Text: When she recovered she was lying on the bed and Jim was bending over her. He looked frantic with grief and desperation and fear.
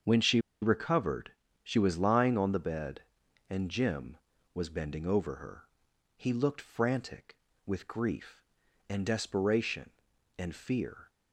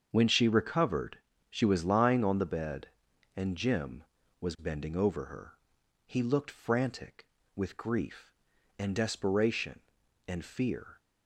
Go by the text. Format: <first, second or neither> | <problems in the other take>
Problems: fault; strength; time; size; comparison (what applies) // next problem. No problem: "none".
second | starts louder than the rest; until 1.2 s; 7 dB; also in the second // pauses between "she" and "recovered"; slight; at 0.3 s; 0.23 s long // pauses between "recovered" and "she"; slight; at 1.3 s; 0.32 s long; slight in the second